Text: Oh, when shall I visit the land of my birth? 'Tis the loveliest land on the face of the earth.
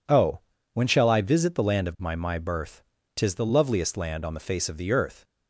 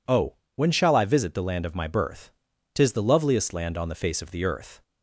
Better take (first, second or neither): second